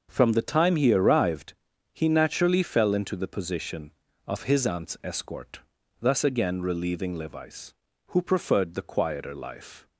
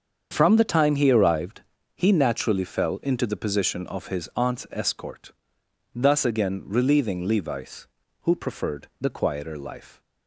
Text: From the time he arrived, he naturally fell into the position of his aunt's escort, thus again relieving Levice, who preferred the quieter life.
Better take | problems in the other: neither | starts louder than the rest; the same in both

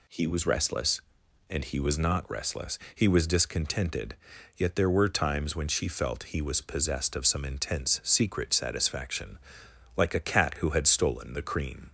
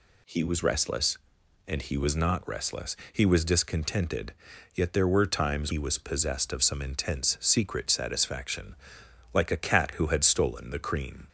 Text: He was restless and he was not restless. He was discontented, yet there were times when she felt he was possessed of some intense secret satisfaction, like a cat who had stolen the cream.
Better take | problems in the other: first | skips "when she felt"; at 5.7 s

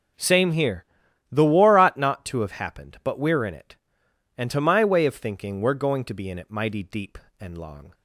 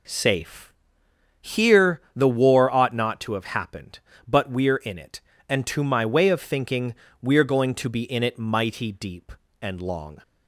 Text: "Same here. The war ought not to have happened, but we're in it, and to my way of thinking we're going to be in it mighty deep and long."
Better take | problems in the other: first | says "Safe" for "Same"; at 0.0 s // pauses between "thinking" and "we're"; slight; at 6.9 s; 0.26 s long

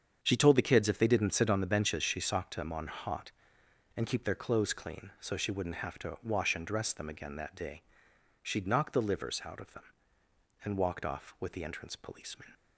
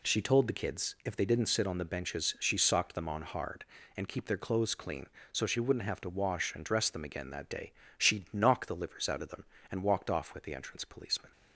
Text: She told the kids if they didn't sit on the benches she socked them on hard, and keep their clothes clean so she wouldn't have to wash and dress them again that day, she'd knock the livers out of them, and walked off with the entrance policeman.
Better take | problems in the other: second | starts louder than the rest; strong; until 1.2 s; 7.5 dB // says "hot" for "hard"; at 2.8 s

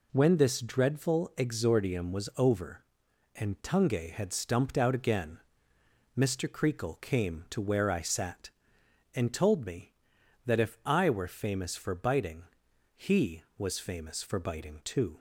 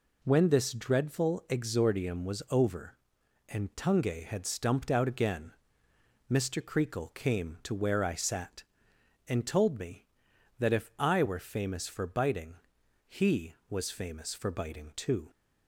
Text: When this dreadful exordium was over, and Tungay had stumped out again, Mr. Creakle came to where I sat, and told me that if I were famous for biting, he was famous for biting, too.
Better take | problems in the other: neither | none

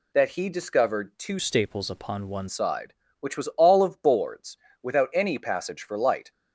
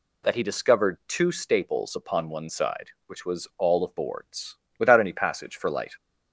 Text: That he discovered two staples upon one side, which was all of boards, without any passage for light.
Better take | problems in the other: second | changes voice from "staples" to "one"; from 1.3 to 2.4 s; 1.1 s long

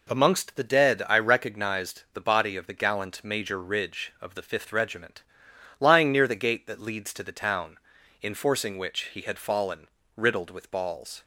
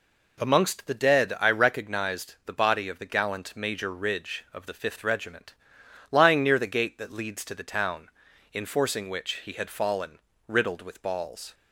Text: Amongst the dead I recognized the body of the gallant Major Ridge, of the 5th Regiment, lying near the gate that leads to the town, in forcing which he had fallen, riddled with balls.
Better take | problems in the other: neither | none

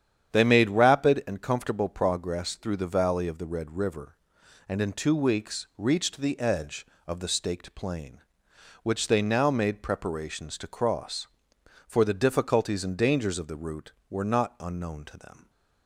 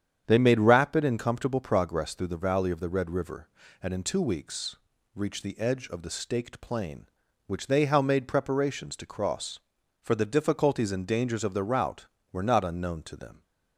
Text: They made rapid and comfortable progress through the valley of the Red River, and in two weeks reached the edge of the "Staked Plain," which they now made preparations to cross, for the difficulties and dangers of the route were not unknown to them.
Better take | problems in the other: first | starts louder than the rest; strong; until 1.2 s; 8.5 dB; strong in the first // pauses between "weeks" and "reached"; at 4.7 s; 0.38 s long // says "how" for "now"; at 7.8 s

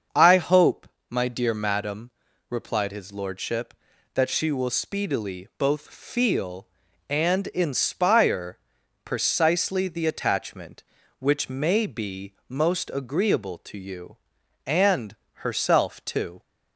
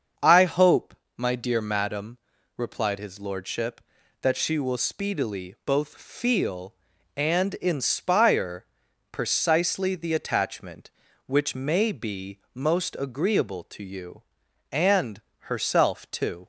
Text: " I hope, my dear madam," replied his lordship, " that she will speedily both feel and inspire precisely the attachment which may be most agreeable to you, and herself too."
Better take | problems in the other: neither | starts louder than the rest; the same in both // pauses between "inspire" and "precisely"; noticeable; the same in both // pauses between "be" and "most"; slight; the same in both // pauses between "and" and "herself"; slight; the same in both

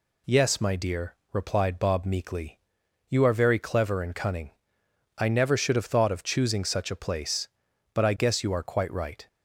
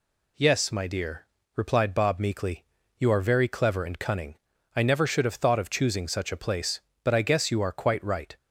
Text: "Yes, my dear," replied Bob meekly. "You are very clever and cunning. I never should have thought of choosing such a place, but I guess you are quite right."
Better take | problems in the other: neither | none

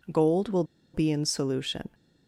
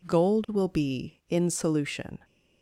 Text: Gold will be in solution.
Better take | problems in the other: second | pauses between "will" and "be"; slight; at 0.6 s; 0.30 s long

